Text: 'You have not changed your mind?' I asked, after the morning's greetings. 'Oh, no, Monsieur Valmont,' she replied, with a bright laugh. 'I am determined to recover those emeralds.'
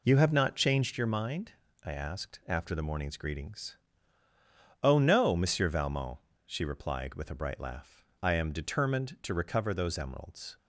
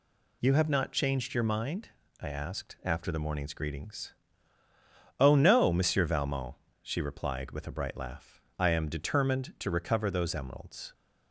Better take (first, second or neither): second